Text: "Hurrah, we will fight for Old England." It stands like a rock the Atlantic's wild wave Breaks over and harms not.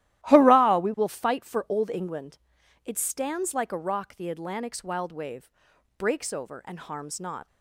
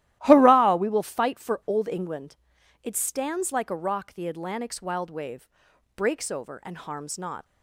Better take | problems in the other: neither | starts louder than the rest; strong; the same in both // pauses between "wave" and "Breaks"; noticeable; the same in both

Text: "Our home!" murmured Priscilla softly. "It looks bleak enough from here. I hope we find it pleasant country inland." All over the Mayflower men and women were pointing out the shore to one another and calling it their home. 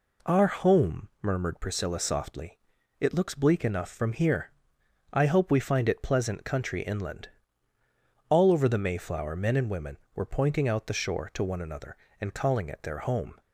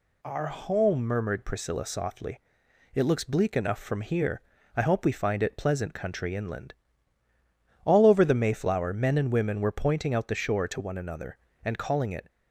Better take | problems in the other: first | stops before "their home"; at 12.2 s

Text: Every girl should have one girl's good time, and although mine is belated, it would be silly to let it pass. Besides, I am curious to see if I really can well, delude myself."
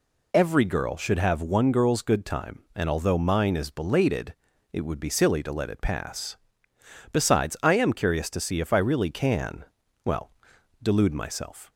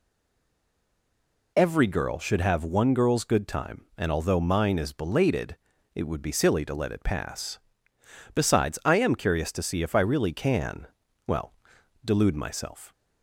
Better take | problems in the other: first | stays silent before the first word; noticeable; until 1.5 s; 1.5 s long // pauses between "can" and "well"; at 10.8 s; 0.40 s long; also in the first

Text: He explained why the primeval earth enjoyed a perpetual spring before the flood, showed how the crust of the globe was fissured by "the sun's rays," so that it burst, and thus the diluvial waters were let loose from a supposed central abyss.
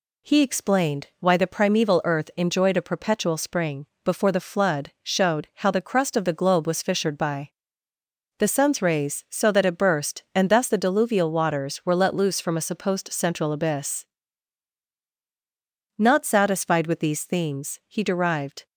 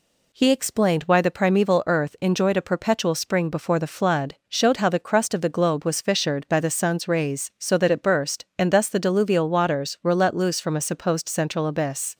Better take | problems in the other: second | pauses between "spring" and "before"; slight; at 3.8 s; 0.20 s long // pauses between "by" and "the"; noticeable; at 7.4 s; 0.88 s long // goes on to say "Not satisfied with these themes he derived"; strong; from 15.9 s on; 2.6 s long

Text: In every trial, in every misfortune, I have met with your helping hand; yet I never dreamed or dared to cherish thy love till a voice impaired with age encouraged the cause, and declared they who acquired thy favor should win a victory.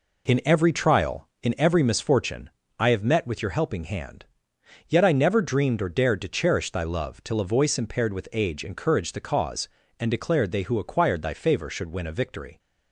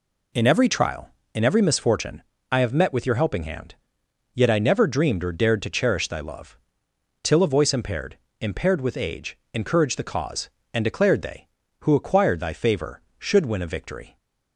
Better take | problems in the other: first | pauses between "love" and "till"; noticeable; at 6.5 s; 0.66 s long // says "impaired" twice; at 8.4 s // pauses between "age" and "encouraged"; slight; at 9.3 s; 0.16 s long

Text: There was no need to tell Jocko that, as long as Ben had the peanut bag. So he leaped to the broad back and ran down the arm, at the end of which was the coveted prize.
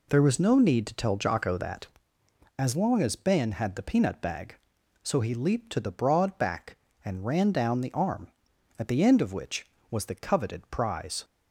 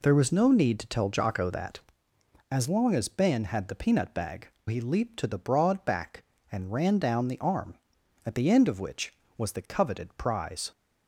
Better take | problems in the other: first | skips "So"; at 4.5 s

